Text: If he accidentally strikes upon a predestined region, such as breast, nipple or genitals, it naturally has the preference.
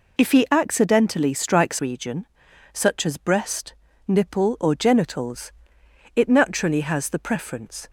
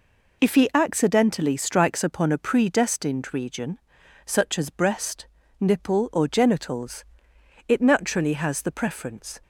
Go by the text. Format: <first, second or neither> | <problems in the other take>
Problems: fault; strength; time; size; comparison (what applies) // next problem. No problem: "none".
second | skips "upon a predestined"; at 1.7 s